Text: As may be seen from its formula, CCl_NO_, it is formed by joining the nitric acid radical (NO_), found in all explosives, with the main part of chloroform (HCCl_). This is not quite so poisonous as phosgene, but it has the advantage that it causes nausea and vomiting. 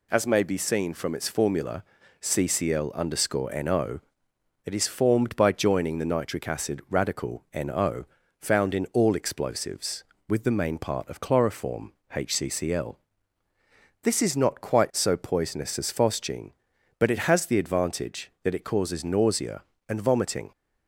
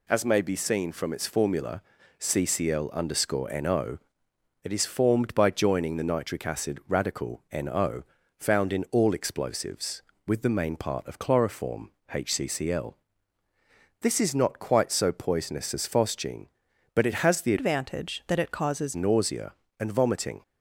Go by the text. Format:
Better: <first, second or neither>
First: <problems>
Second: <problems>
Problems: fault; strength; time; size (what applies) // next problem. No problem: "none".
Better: first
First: none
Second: changes voice from "advantage" to "causes"; from 17.5 to 18.9 s; 1.4 s long